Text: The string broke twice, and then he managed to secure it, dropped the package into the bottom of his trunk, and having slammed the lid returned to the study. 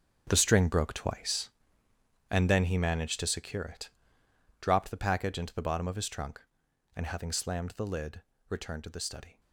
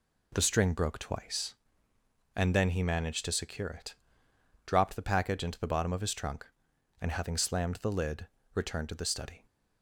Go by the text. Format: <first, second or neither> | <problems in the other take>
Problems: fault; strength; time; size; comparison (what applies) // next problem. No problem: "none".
second | gets quieter; strong; throughout; 13 dB // pauses between "lid" and "returned"; slight; at 8.2 s; 0.28 s long; slight in the second